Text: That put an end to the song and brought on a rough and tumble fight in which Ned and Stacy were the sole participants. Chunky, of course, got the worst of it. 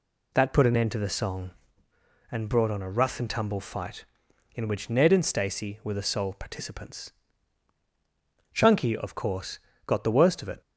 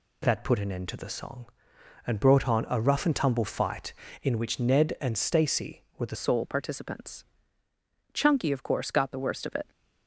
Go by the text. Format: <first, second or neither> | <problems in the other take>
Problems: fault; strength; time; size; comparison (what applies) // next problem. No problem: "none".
first | changes voice at "sole"; from 6.1 s on; 3.5 s long